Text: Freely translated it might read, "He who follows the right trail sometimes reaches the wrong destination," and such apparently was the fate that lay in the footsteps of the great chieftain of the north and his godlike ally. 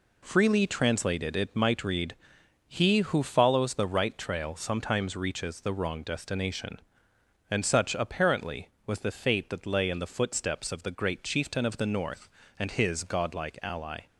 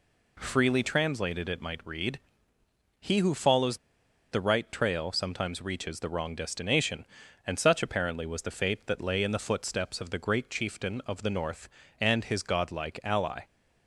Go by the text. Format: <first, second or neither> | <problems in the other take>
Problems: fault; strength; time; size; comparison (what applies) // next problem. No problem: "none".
first | pauses between "follows" and "the"; noticeable; at 3.7 s; 0.53 s long